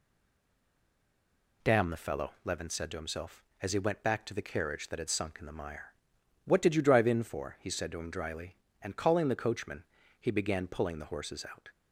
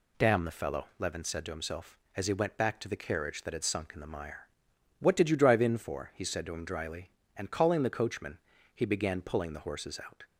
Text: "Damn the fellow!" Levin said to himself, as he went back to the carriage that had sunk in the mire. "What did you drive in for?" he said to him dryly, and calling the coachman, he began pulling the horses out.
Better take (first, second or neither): second